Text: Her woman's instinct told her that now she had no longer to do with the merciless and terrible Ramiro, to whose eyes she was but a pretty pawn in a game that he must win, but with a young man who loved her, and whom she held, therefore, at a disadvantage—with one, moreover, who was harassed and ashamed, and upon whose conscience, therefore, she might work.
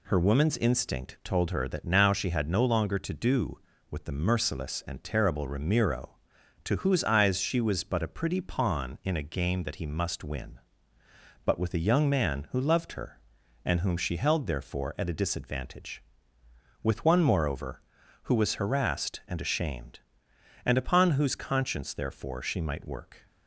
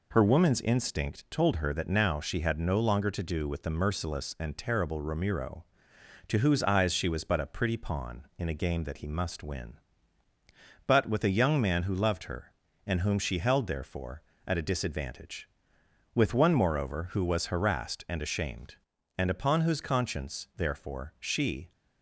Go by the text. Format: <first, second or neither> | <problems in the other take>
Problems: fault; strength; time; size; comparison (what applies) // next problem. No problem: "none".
first | stops before "might work"; at 21.7 s